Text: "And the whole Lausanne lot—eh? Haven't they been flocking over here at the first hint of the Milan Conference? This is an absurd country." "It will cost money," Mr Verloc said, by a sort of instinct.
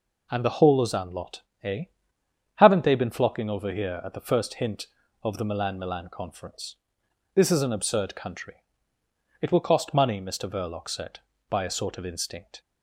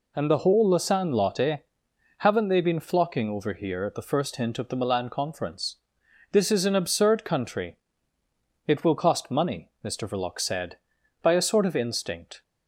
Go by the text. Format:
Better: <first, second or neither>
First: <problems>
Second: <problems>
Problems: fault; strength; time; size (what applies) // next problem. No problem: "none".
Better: second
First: says "Milan" twice; at 5.7 s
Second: none